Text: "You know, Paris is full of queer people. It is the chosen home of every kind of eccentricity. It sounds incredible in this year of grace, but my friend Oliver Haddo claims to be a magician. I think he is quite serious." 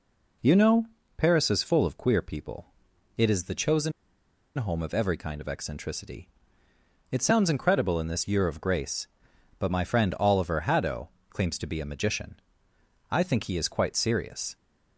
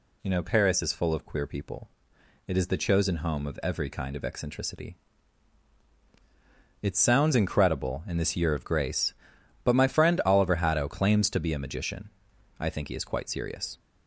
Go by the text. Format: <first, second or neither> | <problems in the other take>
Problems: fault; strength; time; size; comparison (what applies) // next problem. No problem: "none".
second | pauses between "chosen" and "home"; noticeable; at 3.9 s; 0.66 s long // pauses between "Haddo" and "claims"; slight; at 11.0 s; 0.22 s long